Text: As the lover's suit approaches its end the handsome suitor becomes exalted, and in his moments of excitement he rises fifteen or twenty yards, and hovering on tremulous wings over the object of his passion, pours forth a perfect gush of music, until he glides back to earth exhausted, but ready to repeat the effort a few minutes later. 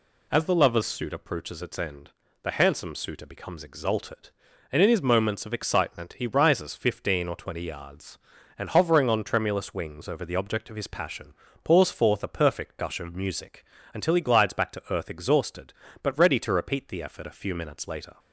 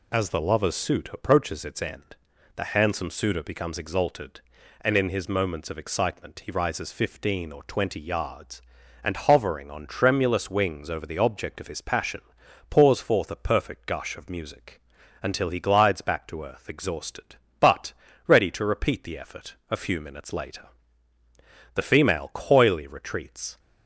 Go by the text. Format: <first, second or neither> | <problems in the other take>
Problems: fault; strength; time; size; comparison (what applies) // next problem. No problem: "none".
first | pauses between "end" and "the"; at 2.1 s; 0.40 s long; slight in the first // pauses between "but" and "ready"; slight; at 17.9 s; 0.34 s long // pauses between "effort" and "a"; slight; at 19.5 s; 0.16 s long // goes on to say "The female coyly retreats"; strong; from 21.7 s on; 1.8 s long